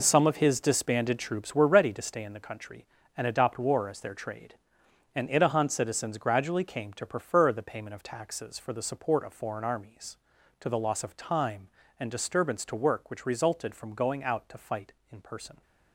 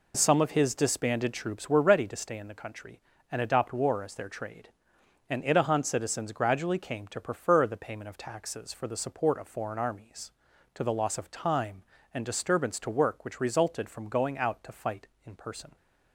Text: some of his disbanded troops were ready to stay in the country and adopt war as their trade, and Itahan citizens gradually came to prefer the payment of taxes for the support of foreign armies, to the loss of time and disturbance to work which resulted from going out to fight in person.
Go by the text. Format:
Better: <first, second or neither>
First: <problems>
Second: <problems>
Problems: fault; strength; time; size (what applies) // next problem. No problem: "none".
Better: second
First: gets quieter; strong; throughout; 10 dB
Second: none